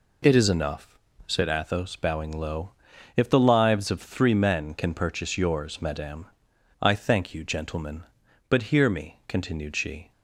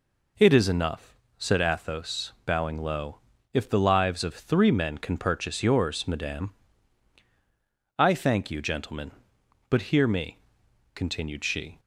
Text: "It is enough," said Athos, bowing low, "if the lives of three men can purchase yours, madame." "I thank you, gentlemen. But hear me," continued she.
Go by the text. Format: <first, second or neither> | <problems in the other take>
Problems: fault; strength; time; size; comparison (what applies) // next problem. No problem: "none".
neither | none